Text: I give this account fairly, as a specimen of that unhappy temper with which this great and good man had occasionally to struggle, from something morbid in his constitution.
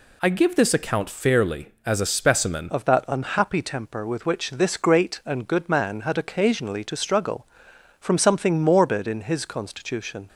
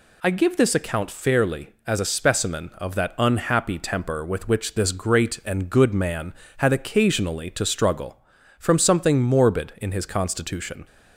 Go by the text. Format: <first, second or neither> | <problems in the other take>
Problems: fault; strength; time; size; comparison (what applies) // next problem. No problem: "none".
second | changes voice at "of"; from 2.6 s on; 7.6 s long